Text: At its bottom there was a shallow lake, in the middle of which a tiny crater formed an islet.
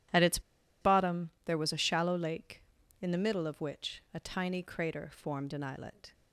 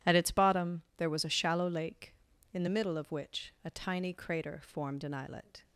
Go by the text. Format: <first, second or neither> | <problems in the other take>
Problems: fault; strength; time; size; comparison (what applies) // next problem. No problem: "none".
second | pauses between "its" and "bottom"; at 0.3 s; 0.41 s long // pauses between "bottom" and "there"; slight; at 1.2 s; 0.16 s long; slight in the second